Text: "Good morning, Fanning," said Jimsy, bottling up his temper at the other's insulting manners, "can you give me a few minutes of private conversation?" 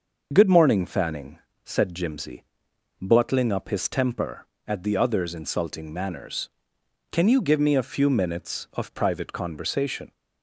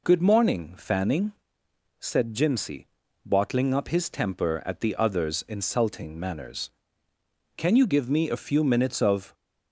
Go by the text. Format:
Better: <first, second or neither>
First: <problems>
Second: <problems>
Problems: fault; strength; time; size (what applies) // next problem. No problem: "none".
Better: first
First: none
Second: stops before "private conversation"; at 9.3 s